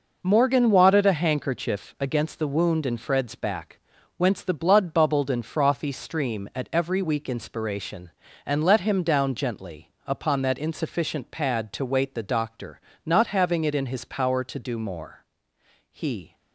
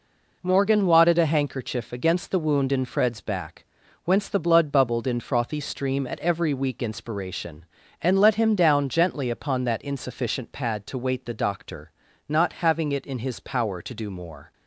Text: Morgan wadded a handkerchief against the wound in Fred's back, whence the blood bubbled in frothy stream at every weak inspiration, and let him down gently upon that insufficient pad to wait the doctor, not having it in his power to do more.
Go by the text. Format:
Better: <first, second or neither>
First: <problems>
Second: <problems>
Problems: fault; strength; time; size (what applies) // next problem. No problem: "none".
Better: second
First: pauses between "gently" and "upon"; slight; at 9.9 s; 0.16 s long // goes on to say "He"; slight; from 15.8 s on; 0.46 s long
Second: none